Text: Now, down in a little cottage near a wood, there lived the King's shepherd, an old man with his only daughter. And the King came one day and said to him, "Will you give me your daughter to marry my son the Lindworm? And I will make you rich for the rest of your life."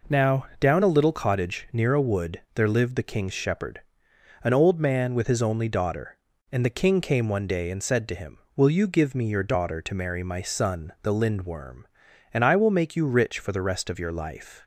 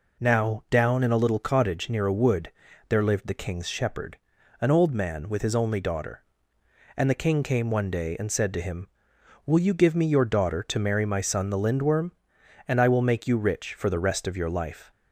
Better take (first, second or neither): second